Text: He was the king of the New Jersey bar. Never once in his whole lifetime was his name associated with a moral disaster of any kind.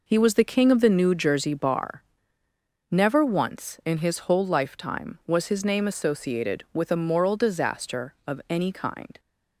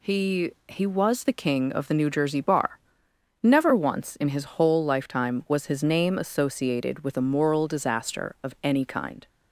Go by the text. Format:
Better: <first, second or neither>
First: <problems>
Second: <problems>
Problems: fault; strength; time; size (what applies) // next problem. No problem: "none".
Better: first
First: none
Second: says "He" twice; at 0.6 s